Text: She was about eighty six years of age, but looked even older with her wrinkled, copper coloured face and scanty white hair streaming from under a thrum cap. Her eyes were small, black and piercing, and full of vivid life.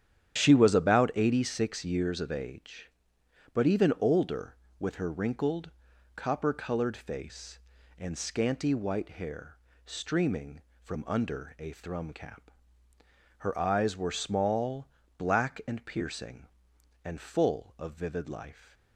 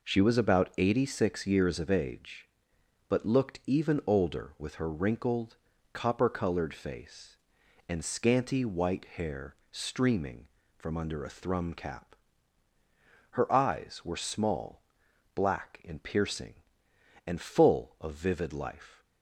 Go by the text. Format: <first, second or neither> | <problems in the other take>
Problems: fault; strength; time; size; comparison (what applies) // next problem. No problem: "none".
second | starts louder than the rest; strong; until 1.4 s; 10 dB // skips "looked"; at 3.6 s // pauses between "hair" and "streaming"; slight; at 9.5 s; 0.30 s long; slight in the second